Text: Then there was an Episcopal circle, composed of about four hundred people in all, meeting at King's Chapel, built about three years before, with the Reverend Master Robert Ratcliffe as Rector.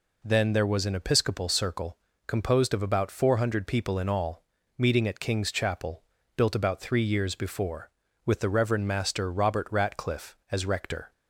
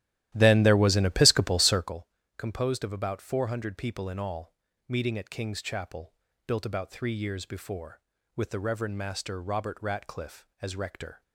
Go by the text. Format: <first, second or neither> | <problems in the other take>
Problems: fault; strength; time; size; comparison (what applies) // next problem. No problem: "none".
first | starts louder than the rest; strong; until 2.0 s; 13.5 dB